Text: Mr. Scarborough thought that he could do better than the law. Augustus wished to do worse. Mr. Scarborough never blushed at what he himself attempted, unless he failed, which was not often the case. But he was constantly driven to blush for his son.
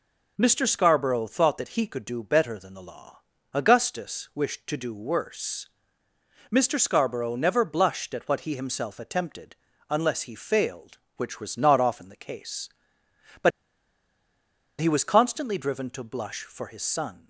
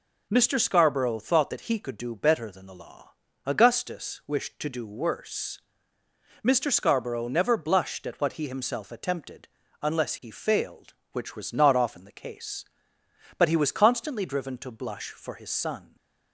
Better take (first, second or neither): second